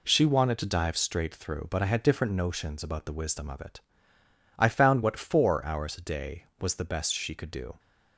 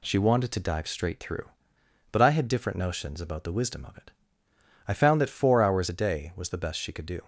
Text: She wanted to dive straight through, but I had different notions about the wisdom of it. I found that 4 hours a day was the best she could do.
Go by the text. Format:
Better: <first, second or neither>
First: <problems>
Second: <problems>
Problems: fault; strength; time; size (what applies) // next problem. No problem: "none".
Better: second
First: says "what" for "that"; at 5.0 s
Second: none